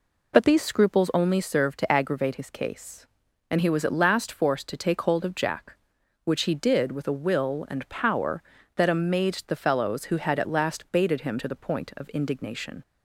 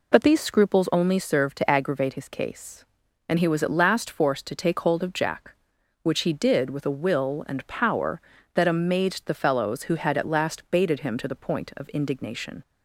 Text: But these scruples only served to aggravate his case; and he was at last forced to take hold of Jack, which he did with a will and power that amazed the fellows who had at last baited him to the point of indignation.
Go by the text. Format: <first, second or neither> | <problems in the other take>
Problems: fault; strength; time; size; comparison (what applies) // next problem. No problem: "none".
neither | none